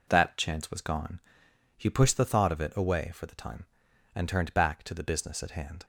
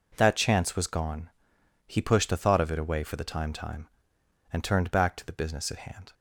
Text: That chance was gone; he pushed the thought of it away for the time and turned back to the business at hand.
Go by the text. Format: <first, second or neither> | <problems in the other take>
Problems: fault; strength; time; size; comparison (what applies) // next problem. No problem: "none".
first | says "time" twice; at 3.5 s